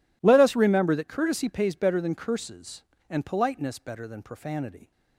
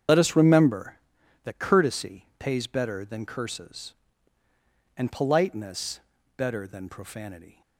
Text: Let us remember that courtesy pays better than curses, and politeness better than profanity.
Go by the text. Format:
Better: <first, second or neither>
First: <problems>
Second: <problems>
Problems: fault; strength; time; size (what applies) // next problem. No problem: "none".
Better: first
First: none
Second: loses the start of "Let"; at 0.0 s; 60 ms // starts louder than the rest; strong; until 1.5 s; 8 dB // pauses between "politeness" and "better"; at 5.9 s; 0.38 s long